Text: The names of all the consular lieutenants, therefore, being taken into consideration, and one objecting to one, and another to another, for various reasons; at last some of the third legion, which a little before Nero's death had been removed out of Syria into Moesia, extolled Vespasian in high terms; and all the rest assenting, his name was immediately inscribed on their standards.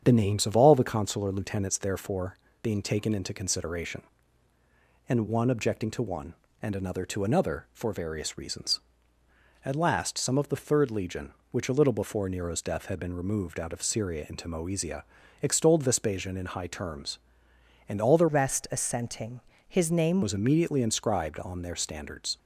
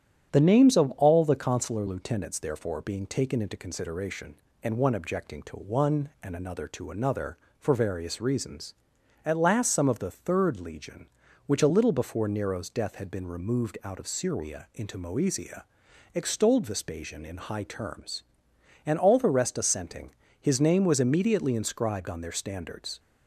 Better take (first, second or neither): second